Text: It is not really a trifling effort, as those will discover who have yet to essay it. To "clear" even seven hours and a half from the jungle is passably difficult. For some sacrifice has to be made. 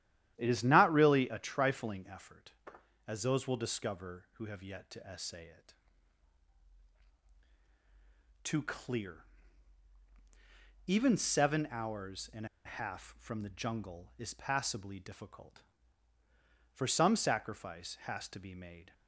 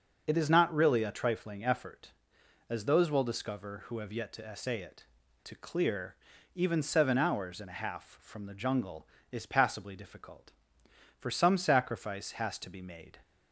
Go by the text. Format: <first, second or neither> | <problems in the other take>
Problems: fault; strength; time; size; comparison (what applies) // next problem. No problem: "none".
second | starts louder than the rest; strong; until 1.3 s; 12 dB; also in the second // pauses between "clear" and "even"; strong; at 9.2 s; 1.6 s long; also in the second // pauses between "and" and "a"; slight; at 12.4 s; 0.19 s long